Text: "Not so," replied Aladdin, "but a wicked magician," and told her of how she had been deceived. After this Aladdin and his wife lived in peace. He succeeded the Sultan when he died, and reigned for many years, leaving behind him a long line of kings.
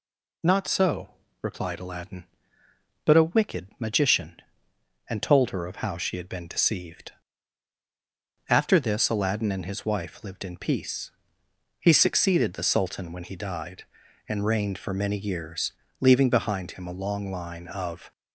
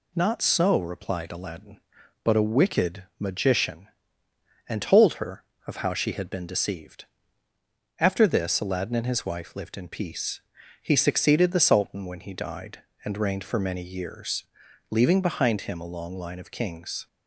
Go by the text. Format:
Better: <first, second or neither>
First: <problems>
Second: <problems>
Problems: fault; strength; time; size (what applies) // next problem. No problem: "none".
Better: second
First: stops before "kings"; at 18.1 s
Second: none